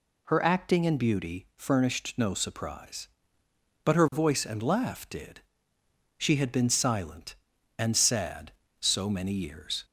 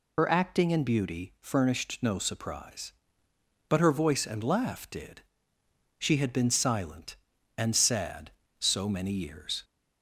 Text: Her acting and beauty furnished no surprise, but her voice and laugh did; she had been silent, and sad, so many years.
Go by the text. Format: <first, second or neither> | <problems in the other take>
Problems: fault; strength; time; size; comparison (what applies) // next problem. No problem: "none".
first | loses the start of "Her"; at 0.1 s; 45 ms